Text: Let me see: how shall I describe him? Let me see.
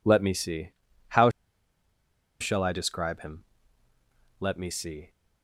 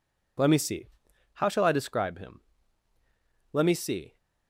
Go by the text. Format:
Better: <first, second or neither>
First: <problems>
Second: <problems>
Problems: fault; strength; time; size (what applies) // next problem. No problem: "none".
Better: second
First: pauses between "how" and "shall"; at 1.2 s; 1.1 s long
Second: none